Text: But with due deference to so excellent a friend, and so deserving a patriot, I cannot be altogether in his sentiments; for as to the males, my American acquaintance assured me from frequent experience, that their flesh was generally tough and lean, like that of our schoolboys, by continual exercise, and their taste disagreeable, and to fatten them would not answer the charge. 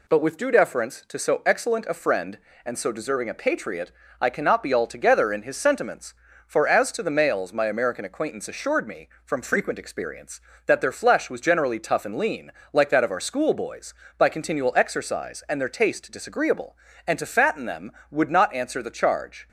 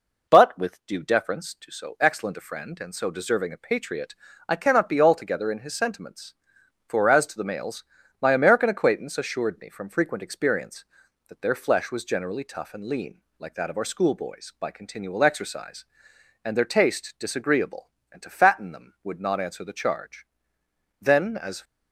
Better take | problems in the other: first | goes on to say "Then as"; noticeable; from 20.9 s on; 0.64 s long

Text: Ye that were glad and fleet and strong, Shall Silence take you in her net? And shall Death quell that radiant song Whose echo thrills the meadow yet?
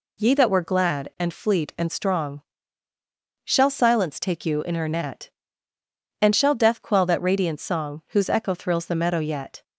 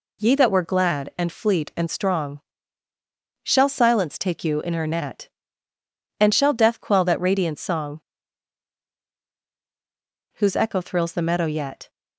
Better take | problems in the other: first | pauses between "song" and "Whose"; strong; at 8.0 s; 2.3 s long

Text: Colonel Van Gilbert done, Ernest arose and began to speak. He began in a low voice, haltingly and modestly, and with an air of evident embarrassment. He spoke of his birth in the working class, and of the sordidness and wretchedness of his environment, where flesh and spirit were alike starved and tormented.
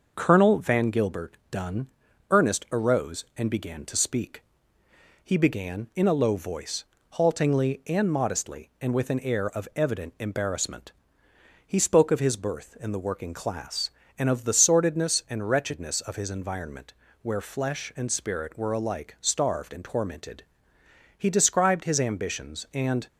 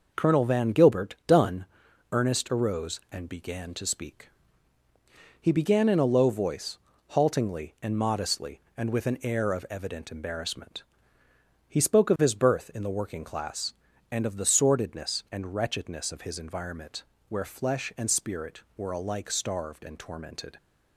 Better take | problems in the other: second | starts louder than the rest; noticeable; until 1.1 s; 6 dB // goes on to say "He described his ambitions and"; strong; from 21.1 s on; 1.9 s long

